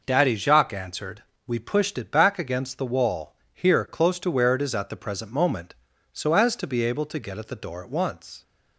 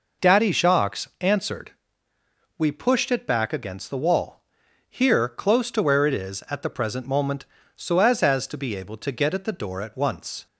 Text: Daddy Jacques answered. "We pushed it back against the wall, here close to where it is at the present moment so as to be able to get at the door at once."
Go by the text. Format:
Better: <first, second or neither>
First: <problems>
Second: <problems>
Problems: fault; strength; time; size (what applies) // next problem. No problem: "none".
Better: first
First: none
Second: pauses between "Jacques" and "answered"; slight; at 1.0 s; 0.16 s long // says "as" twice; at 8.2 s